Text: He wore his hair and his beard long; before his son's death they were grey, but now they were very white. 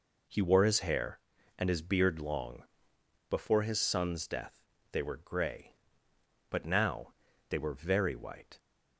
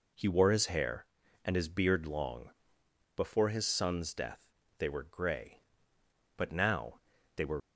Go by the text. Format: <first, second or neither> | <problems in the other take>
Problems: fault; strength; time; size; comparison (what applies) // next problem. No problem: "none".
first | pauses between "death" and "they"; slight; at 4.4 s; 0.32 s long; slight in the first // pauses between "now" and "they"; slight; at 7.0 s; 0.34 s long; slight in the first // stops before "very white"; at 7.6 s